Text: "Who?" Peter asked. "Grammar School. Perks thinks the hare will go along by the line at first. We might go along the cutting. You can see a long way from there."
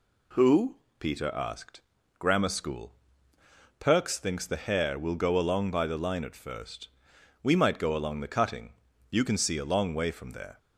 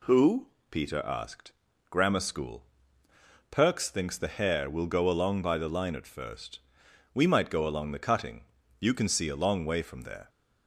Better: neither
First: none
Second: none

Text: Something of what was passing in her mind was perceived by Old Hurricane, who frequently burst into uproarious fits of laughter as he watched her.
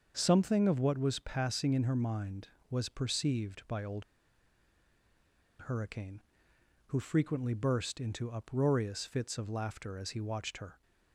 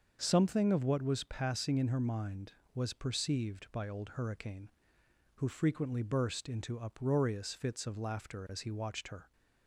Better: second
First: starts louder than the rest; until 1.1 s; 6.5 dB // pauses between "Old" and "Hurricane"; strong; at 4.0 s; 1.5 s long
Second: starts louder than the rest; until 1.2 s; 6.5 dB

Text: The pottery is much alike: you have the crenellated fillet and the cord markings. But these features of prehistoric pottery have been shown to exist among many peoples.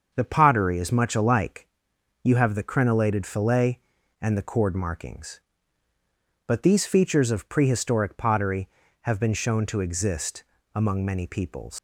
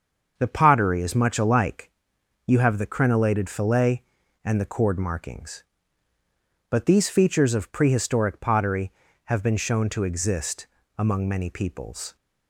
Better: second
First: starts louder than the rest; until 1.1 s; 6.5 dB // pauses between "exist" and "among"; slight; at 10.4 s; 0.32 s long // leaves "peoples" unfinished; at 11.7 s; 135 ms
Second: starts louder than the rest; until 1.3 s; 6.5 dB // pauses between "exist" and "among"; slight; at 10.6 s; 0.32 s long

